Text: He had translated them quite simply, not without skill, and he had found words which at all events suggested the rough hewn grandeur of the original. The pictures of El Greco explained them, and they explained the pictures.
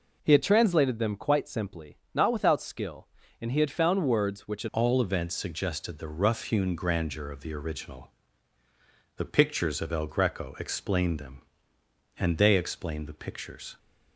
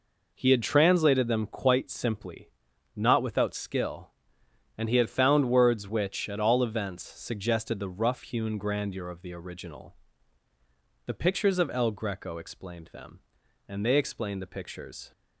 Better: second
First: changes voice at "all"; from 4.7 s on; 9.0 s long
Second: none

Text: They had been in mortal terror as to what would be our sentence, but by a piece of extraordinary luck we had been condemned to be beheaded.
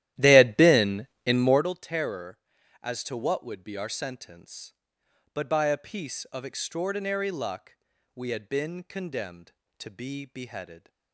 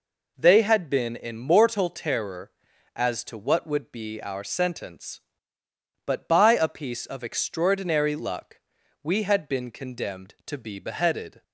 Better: second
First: starts louder than the rest; strong; until 1.6 s; 13.5 dB // pauses between "luck" and "we"; at 7.7 s; 0.38 s long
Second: pauses between "luck" and "we"; at 8.5 s; 0.44 s long

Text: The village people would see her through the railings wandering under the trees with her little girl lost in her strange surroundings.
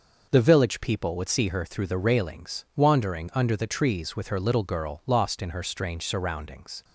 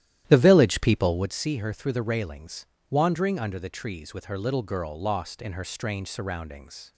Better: first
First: none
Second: starts louder than the rest; strong; until 1.4 s; 12.5 dB // pauses between "railings" and "wandering"; slight; at 2.6 s; 0.24 s long

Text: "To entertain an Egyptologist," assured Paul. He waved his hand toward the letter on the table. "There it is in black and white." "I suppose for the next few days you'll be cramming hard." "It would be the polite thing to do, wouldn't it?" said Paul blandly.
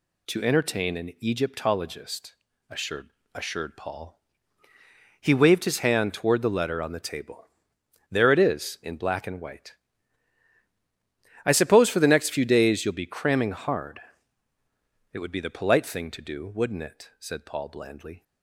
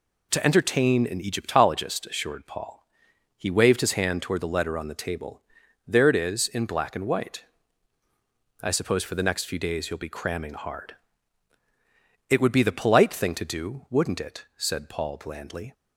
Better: second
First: says "assured" twice; at 3.3 s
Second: none

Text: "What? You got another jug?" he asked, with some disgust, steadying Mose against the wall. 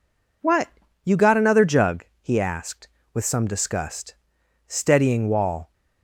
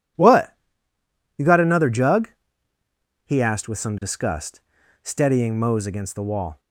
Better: second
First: skips "Mose against the"; at 5.2 s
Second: none

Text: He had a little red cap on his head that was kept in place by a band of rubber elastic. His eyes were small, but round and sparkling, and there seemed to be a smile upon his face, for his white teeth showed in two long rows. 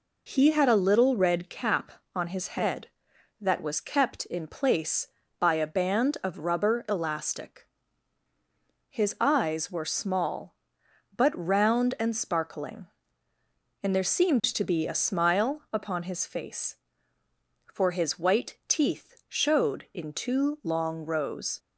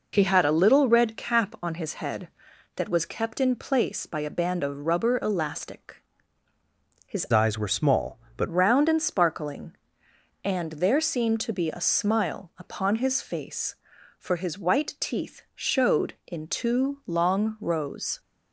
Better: first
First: none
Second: changes voice from "eyes" to "but"; from 7.3 to 8.4 s; 1.1 s long

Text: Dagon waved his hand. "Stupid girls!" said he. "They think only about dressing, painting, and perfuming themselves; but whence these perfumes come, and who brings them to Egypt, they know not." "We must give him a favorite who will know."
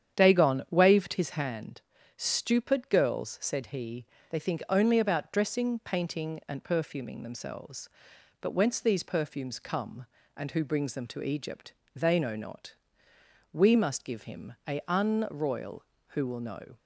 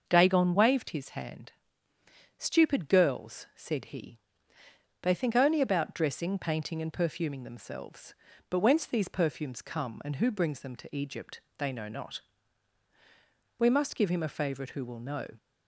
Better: second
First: starts louder than the rest; strong; until 1.2 s; 9 dB // says "unroyal" for "favorite"; at 14.8 s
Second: starts louder than the rest; until 1.1 s; 6 dB

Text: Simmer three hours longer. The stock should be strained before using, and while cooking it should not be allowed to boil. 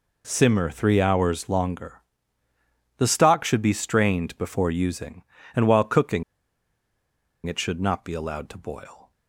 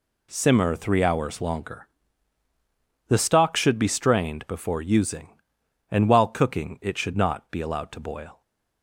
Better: second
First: pauses between "cooking" and "it"; at 6.2 s; 1.2 s long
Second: none

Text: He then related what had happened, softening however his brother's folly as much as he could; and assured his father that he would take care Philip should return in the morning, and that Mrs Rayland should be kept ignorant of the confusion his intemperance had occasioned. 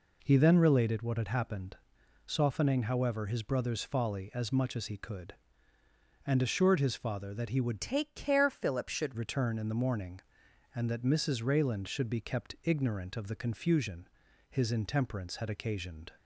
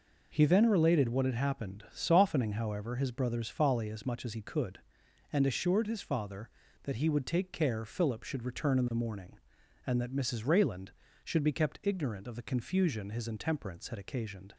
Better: second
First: changes voice from "take" to "should"; from 7.8 to 9.1 s; 1.3 s long // pauses between "confusion" and "his"; at 14.0 s; 0.42 s long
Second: none

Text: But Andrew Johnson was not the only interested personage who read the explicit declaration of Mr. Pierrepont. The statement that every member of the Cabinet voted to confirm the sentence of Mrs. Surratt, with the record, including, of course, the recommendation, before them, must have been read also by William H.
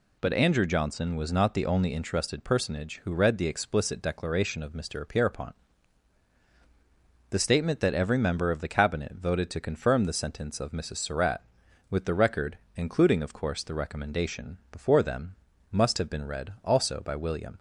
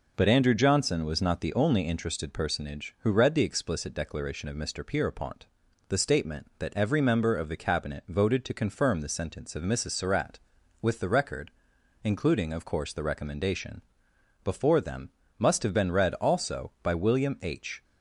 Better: second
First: stops before "H"; at 17.5 s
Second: none

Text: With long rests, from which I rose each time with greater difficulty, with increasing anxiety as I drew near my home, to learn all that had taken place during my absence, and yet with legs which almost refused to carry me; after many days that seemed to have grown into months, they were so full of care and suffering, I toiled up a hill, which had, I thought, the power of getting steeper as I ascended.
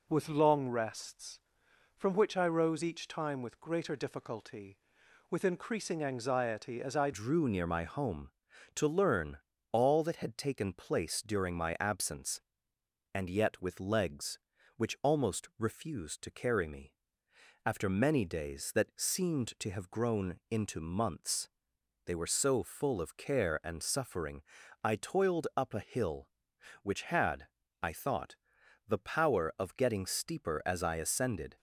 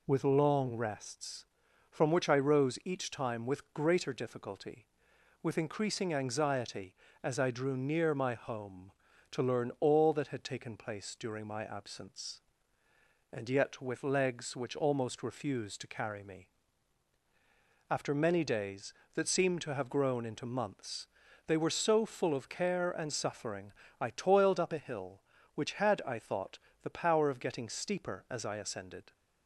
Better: second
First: changes voice at "drew"; from 7.1 s on; 24.4 s long // pauses between "learn" and "all"; slight; at 9.3 s; 0.32 s long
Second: none

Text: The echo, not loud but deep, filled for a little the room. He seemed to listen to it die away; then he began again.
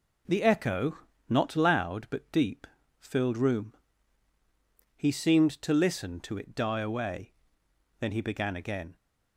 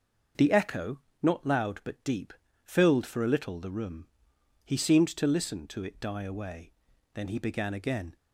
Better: second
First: skips "for a little the"; at 3.3 s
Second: none

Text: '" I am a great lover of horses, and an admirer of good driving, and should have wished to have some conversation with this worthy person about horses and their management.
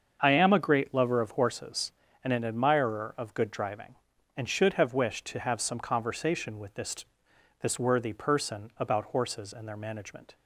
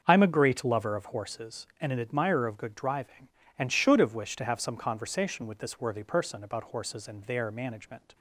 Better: second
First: starts louder than the rest; until 1.2 s; 7 dB // says "this" twice; at 7.6 s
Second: starts louder than the rest; until 1.0 s; 7 dB

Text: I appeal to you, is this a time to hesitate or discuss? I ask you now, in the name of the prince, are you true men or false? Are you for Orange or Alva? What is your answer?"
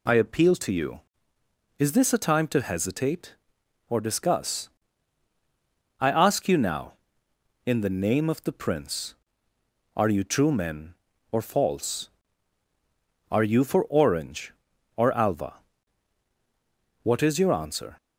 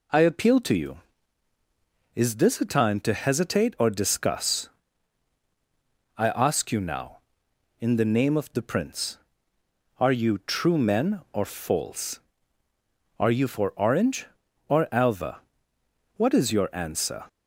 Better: neither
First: none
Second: none

